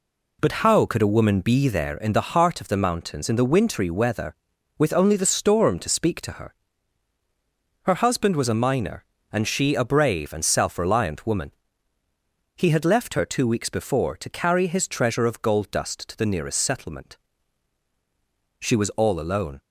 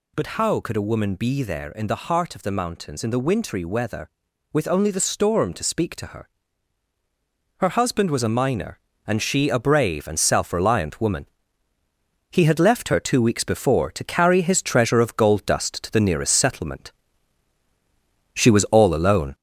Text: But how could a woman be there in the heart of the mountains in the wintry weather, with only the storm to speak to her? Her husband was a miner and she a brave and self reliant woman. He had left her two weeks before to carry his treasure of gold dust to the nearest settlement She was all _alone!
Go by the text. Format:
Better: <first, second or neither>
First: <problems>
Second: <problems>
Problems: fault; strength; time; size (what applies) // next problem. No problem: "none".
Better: first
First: pauses between "settlement" and "She"; strong; at 17.1 s; 1.4 s long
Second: gets louder; noticeable; throughout; 4 dB // pauses between "settlement" and "She"; strong; at 16.9 s; 1.4 s long